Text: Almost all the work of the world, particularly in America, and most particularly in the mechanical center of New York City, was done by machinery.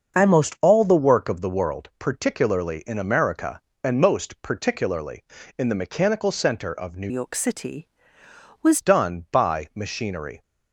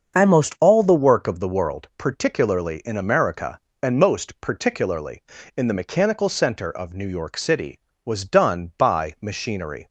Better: second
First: starts louder than the rest; until 1.2 s; 6.5 dB // changes voice from "York" to "was"; from 7.0 to 8.7 s; 1.7 s long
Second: starts louder than the rest; until 1.2 s; 6.5 dB

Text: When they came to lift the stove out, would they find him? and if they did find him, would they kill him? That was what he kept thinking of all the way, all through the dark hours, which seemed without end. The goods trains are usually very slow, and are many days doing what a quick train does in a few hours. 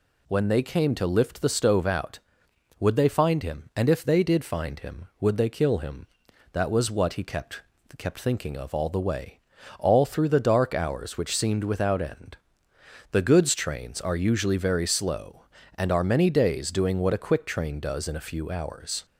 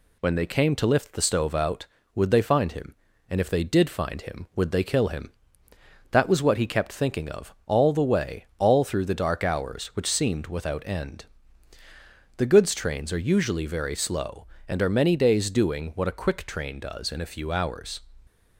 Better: second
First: says "kept" twice; at 7.9 s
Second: none

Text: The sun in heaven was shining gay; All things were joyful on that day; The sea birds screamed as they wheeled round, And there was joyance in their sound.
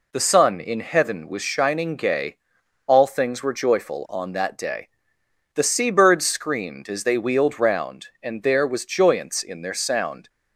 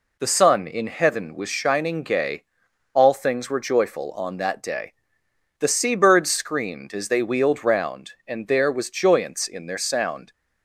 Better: neither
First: none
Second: none

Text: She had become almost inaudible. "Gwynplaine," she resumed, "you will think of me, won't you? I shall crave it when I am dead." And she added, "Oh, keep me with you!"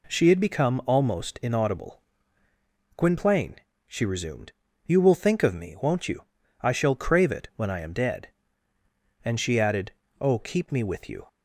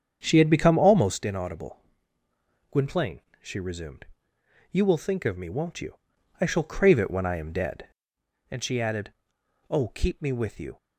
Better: first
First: none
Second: starts louder than the rest; strong; until 1.2 s; 8 dB

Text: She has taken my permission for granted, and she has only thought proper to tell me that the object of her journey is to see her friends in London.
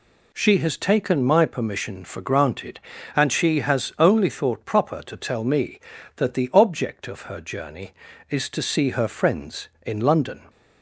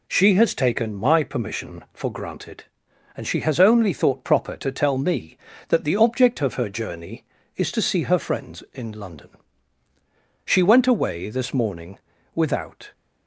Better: first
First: none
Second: goes on to say "She went away this morning without"; strong; from 10.4 s on; 2.4 s long

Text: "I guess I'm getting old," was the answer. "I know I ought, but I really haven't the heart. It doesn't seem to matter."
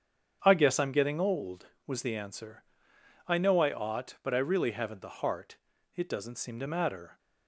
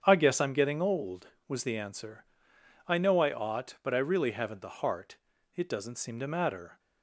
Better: neither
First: starts louder than the rest; strong; until 1.4 s; 8 dB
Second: starts louder than the rest; strong; until 1.0 s; 8 dB

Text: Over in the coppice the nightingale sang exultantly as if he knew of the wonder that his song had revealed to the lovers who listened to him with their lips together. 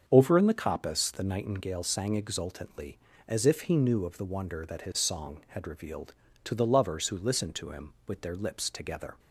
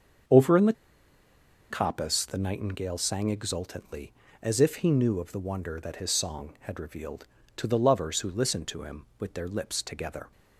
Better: first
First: starts louder than the rest; until 1.0 s; 6.5 dB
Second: starts louder than the rest; until 2.2 s; 6.5 dB // pauses between "the" and "coppice"; noticeable; at 0.7 s; 0.96 s long

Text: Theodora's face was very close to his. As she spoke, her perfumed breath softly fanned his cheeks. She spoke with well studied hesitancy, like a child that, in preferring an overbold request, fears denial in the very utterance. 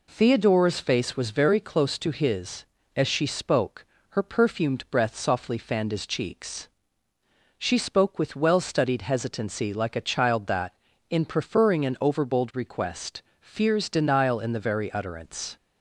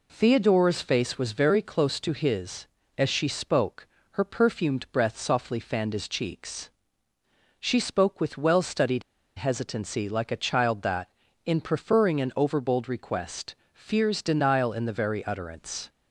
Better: first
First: none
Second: pauses between "studied" and "hesitancy"; slight; at 9.0 s; 0.36 s long

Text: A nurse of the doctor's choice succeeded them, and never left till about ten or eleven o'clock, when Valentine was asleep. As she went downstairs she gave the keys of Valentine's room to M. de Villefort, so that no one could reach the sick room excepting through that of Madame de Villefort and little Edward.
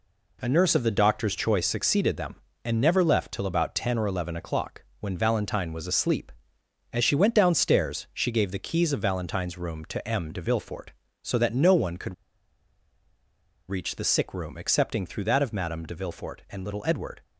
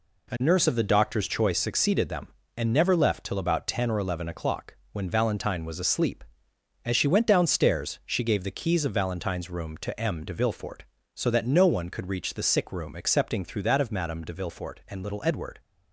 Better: second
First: pauses between "could" and "reach"; strong; at 12.1 s; 1.5 s long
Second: none

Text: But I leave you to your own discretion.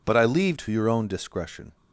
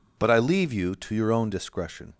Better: second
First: skips "you"; at 0.5 s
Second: none

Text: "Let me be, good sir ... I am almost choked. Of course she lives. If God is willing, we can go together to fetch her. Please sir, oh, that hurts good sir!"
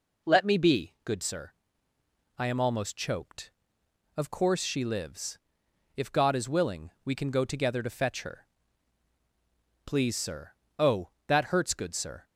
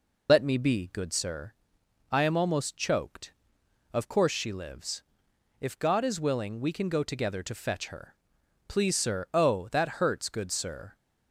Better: first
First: none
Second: loses the start of "Let"; at 0.2 s; 55 ms

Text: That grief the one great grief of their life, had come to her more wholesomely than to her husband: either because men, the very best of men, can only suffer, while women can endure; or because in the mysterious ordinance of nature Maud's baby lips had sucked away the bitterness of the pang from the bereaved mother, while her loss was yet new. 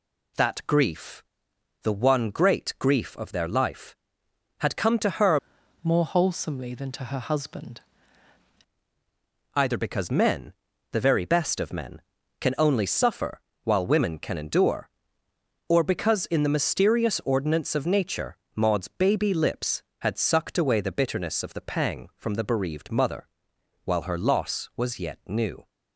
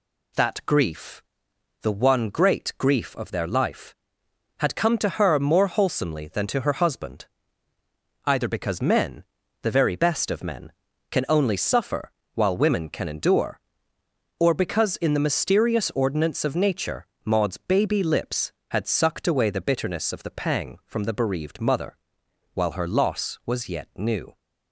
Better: second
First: pauses between "grief" and "the"; noticeable; at 1.2 s; 0.60 s long // changes voice from "more" to "husband"; from 5.8 to 7.8 s; 2.0 s long // pauses between "nature" and "Maud's"; slight; at 18.3 s; 0.18 s long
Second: pauses between "grief" and "the"; noticeable; at 1.2 s; 0.60 s long // pauses between "nature" and "Maud's"; slight; at 17.0 s; 0.18 s long

